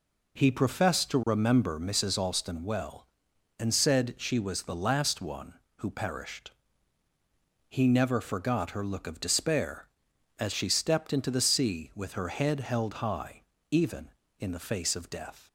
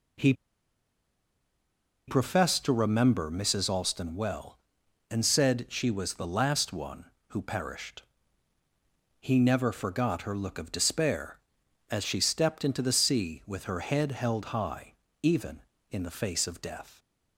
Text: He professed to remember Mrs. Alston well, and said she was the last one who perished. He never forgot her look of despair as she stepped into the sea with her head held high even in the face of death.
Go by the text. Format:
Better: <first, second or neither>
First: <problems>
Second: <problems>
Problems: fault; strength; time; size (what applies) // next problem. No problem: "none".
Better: first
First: pauses between "high" and "even"; slight; at 13.4 s; 0.28 s long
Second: pauses between "He" and "professed"; strong; at 0.3 s; 1.7 s long // pauses between "high" and "even"; slight; at 14.9 s; 0.28 s long